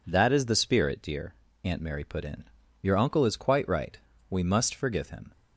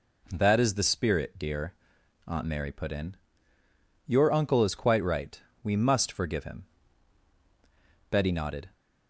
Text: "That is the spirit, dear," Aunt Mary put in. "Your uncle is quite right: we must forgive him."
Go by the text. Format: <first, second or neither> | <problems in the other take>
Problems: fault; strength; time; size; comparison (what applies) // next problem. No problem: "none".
first | goes on to say "Betty nodded"; from 8.0 s on; 0.60 s long